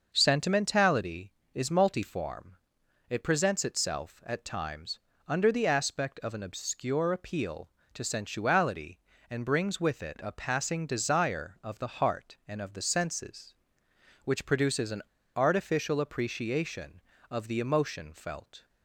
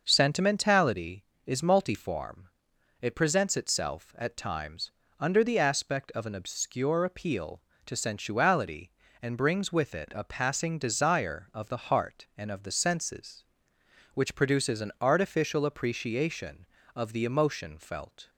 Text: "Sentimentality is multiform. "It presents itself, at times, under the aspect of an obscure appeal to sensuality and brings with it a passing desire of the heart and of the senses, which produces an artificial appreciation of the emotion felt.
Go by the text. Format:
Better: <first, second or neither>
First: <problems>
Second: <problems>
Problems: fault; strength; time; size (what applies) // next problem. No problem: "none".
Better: second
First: starts louder than the rest; until 1.1 s; 6 dB // pauses between "an" and "artificial"; slight; at 14.9 s; 0.34 s long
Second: starts louder than the rest; until 1.0 s; 6 dB